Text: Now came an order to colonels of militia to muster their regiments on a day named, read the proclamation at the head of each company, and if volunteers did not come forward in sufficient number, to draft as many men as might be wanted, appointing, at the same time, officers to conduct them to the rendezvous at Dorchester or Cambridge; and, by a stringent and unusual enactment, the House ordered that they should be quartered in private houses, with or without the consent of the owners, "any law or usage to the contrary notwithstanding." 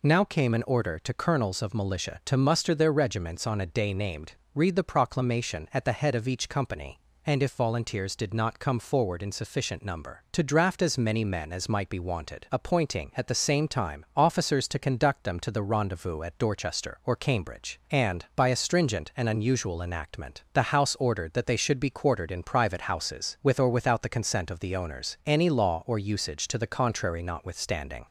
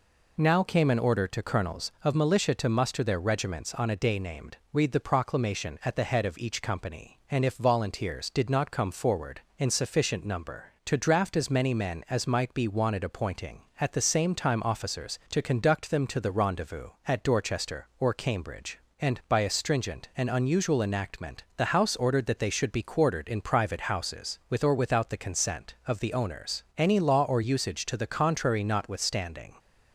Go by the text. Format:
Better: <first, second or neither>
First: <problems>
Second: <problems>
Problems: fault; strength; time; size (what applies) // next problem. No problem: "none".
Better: neither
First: none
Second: none